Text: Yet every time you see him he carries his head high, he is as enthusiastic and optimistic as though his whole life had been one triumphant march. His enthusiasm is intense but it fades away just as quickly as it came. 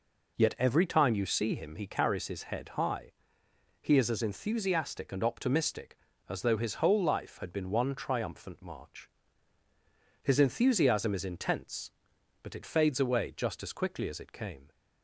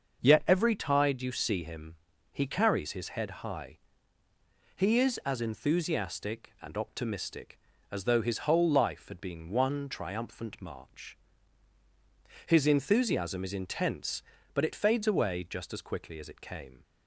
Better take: first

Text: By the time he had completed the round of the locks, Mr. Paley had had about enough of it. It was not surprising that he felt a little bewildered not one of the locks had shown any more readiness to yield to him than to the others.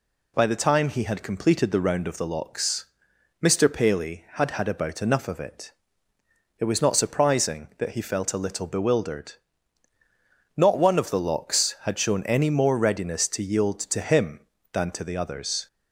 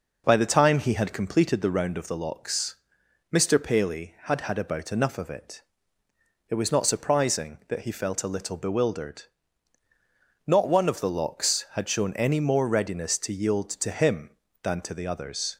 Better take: first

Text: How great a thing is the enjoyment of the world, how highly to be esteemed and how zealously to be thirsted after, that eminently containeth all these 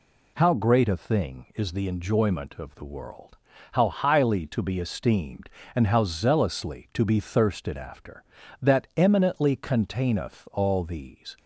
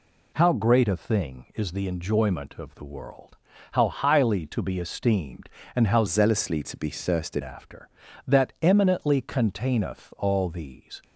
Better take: first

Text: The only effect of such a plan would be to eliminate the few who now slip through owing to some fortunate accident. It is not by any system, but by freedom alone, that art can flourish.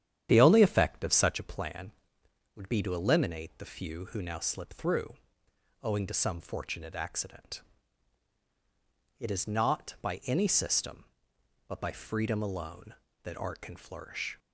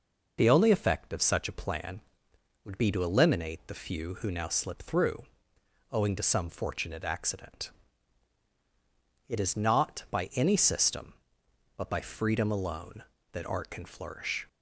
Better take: second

